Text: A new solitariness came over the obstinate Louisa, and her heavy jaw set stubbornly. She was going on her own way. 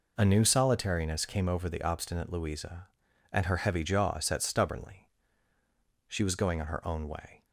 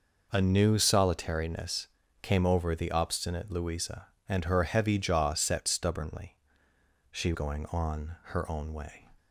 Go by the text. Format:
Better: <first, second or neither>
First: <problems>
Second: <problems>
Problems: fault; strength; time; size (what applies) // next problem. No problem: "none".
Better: first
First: none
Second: pauses between "solitariness" and "came"; slight; at 1.8 s; 0.34 s long // skips "was"; at 7.3 s